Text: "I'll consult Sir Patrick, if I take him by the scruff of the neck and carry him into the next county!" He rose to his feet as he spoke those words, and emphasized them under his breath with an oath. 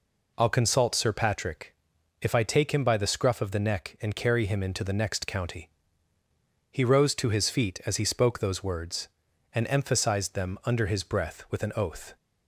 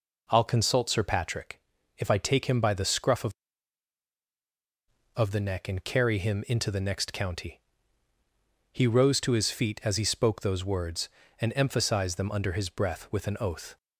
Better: first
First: none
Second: says "of" twice; at 5.1 s

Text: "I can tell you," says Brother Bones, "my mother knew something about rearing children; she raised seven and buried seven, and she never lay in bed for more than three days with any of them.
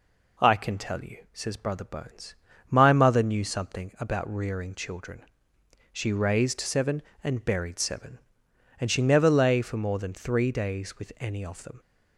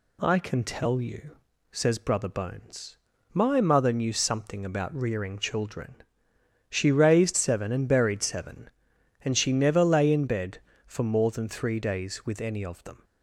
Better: second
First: skips "in bed"; at 9.6 s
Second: none

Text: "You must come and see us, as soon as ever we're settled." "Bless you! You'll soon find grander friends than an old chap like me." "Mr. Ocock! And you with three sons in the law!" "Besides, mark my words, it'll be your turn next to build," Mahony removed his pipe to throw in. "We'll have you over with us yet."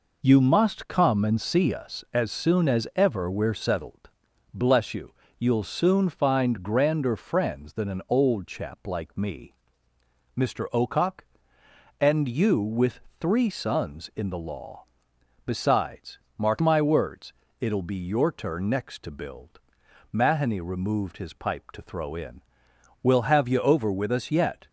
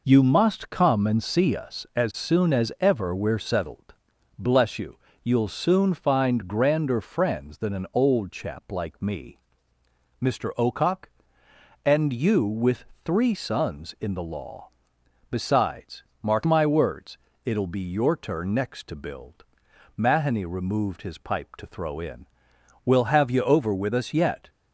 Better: neither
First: pauses between "with" and "three"; slight; at 13.0 s; 0.18 s long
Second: pauses between "with" and "three"; slight; at 12.8 s; 0.18 s long

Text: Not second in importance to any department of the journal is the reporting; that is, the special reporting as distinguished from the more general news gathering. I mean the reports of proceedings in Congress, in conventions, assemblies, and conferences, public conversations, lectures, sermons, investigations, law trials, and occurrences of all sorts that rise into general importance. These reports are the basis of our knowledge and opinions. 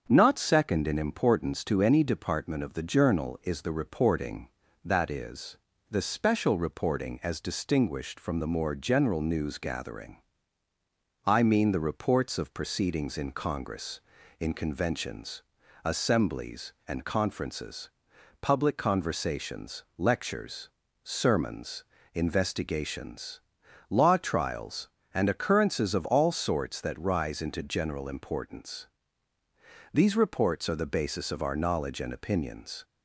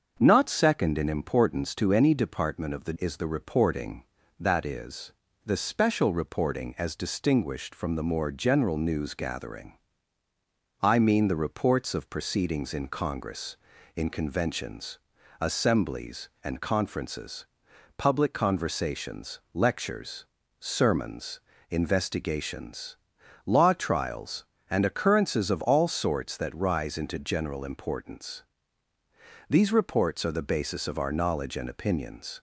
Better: first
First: starts louder than the rest; strong; until 1.0 s; 7 dB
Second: starts louder than the rest; until 1.2 s; 6.5 dB // skips "journal"; at 2.9 s

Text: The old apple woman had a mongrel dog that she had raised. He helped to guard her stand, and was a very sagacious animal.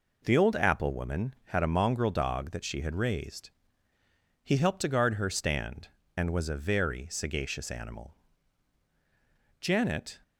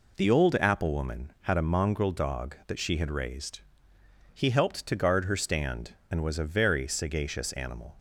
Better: second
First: goes on to say "Janet"; from 9.5 s on; 0.60 s long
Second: none

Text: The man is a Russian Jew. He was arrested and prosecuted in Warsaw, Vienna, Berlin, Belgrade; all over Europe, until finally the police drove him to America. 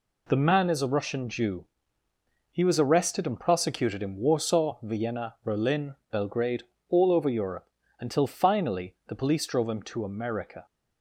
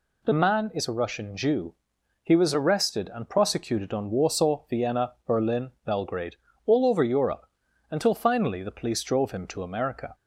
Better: first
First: none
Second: says "on" for "in"; at 3.9 s

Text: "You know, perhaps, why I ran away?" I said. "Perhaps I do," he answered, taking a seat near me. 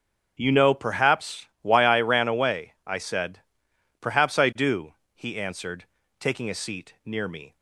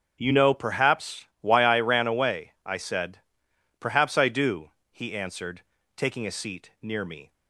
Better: neither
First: starts louder than the rest; strong; until 1.4 s; 7.5 dB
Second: starts louder than the rest; strong; until 1.2 s; 7.5 dB

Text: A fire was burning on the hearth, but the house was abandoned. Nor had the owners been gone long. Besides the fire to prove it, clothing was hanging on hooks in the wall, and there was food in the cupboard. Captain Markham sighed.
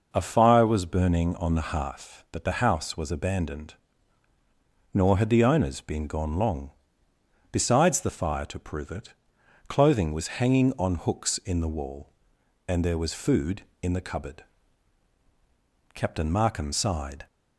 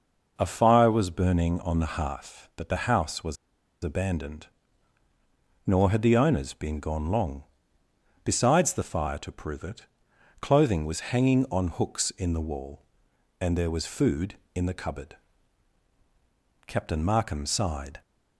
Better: first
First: none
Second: pauses between "was" and "abandoned"; noticeable; at 3.3 s; 0.49 s long

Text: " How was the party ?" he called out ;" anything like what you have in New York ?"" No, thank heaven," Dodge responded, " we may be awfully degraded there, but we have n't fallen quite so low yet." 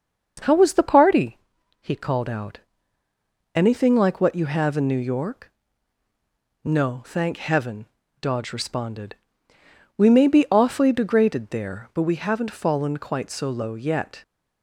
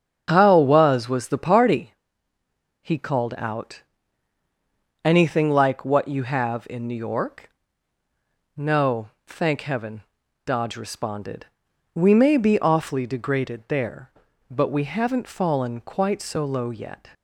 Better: first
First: starts louder than the rest; strong; until 1.6 s; 8 dB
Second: starts louder than the rest; strong; until 1.2 s; 8 dB // says "was" twice; at 1.0 s

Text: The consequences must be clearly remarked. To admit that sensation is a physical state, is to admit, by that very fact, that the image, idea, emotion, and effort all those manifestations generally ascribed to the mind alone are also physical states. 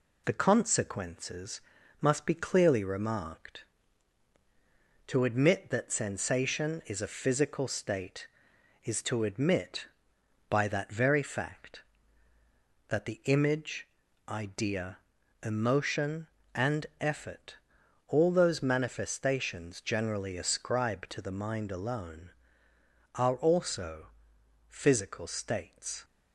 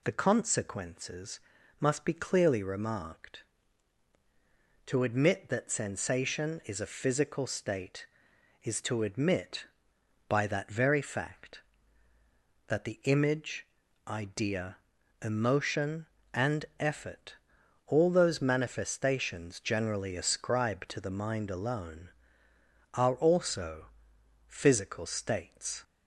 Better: second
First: gets quieter; slight; throughout; 2 dB // pauses between "consequences" and "must"; at 1.5 s; 0.40 s long // pauses between "effort" and "all"; noticeable; at 17.5 s; 0.50 s long // pauses between "also" and "physical"; noticeable; at 24.0 s; 0.62 s long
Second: pauses between "consequences" and "must"; at 1.3 s; 0.40 s long // pauses between "effort" and "all"; noticeable; at 17.3 s; 0.50 s long // pauses between "also" and "physical"; noticeable; at 23.8 s; 0.62 s long

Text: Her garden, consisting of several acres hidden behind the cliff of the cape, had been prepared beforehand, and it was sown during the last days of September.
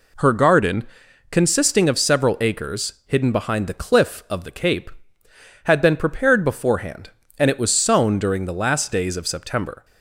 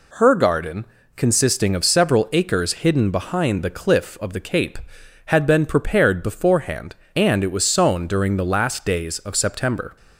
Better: neither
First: none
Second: none

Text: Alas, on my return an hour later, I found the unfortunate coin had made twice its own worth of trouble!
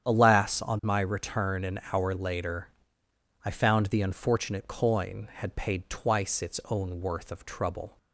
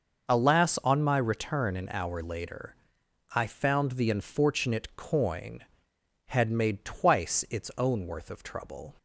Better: second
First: starts louder than the rest; strong; until 1.1 s; 9 dB // says "paid" for "made"; at 5.5 s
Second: starts louder than the rest; noticeable; until 1.3 s; 6 dB

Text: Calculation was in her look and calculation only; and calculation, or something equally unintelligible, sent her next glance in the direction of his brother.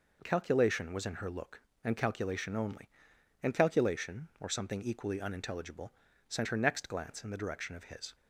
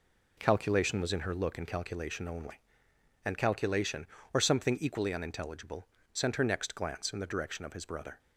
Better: second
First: stops before "brother"; at 8.1 s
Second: none

